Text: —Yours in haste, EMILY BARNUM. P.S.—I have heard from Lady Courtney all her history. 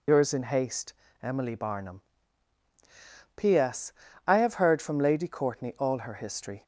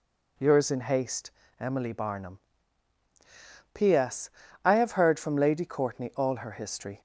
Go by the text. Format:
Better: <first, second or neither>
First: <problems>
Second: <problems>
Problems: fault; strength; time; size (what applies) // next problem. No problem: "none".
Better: second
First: loses the start of "Yours"; at 0.0 s; 70 ms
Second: none